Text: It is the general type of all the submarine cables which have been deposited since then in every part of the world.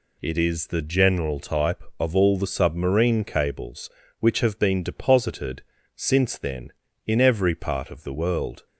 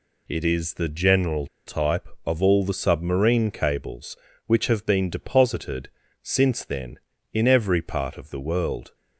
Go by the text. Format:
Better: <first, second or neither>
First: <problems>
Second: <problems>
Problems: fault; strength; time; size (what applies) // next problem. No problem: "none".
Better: first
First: pauses between "deposited" and "since"; slight; at 5.6 s; 0.34 s long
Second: pauses between "general" and "type"; slight; at 1.4 s; 0.20 s long // pauses between "deposited" and "since"; slight; at 5.8 s; 0.34 s long